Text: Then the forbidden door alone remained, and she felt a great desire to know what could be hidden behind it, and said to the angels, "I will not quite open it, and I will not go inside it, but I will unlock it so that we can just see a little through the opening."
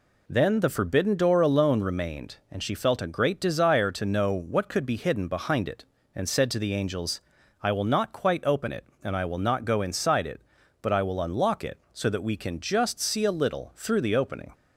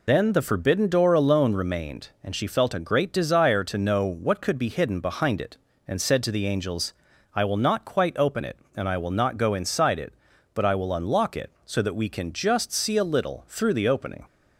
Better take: first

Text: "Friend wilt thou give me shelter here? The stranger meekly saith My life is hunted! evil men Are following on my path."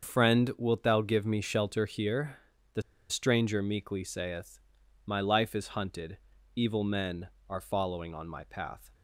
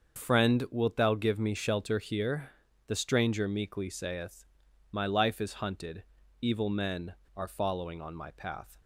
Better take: second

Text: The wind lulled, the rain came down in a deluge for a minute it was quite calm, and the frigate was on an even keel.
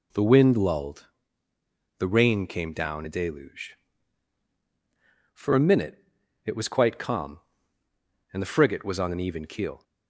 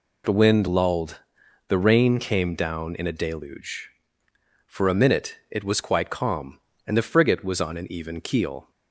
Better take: second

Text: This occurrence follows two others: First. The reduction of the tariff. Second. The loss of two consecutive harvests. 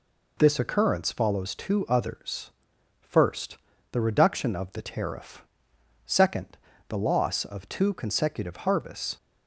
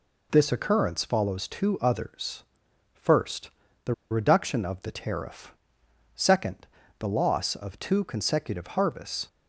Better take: first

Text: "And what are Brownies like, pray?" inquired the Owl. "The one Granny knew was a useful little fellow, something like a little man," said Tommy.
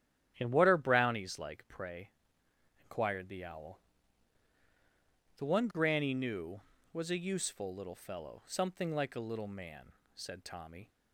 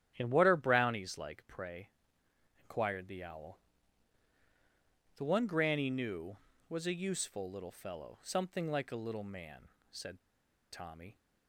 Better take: first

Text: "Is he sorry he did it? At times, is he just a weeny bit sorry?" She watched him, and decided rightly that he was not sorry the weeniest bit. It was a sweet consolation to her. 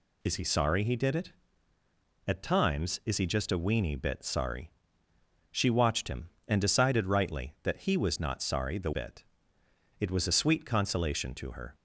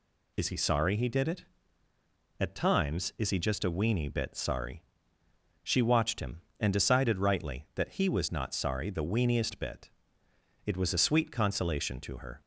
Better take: second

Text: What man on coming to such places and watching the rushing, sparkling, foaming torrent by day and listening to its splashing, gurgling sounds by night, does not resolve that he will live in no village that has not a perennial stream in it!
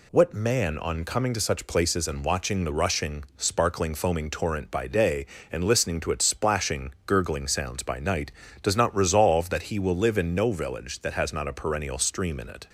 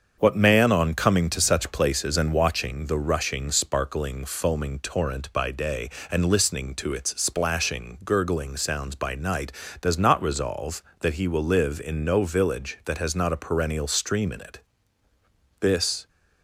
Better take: first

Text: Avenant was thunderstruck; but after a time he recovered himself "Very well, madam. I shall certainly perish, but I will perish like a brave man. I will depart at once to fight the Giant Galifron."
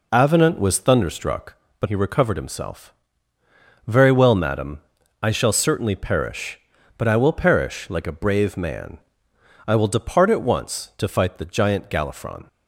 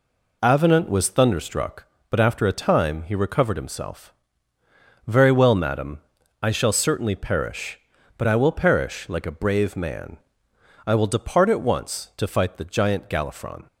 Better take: second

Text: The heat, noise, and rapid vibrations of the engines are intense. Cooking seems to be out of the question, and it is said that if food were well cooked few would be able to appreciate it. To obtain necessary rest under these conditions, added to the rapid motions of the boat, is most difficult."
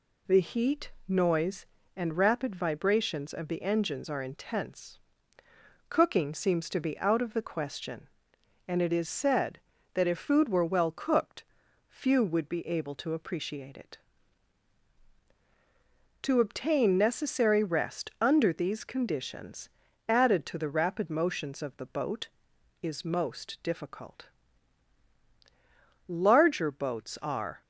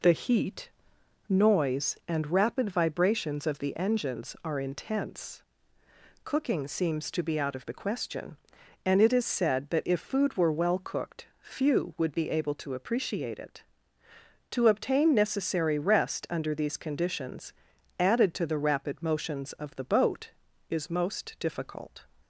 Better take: second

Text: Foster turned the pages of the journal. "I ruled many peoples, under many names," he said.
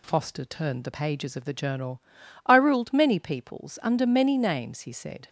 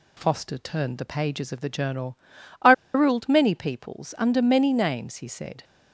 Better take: first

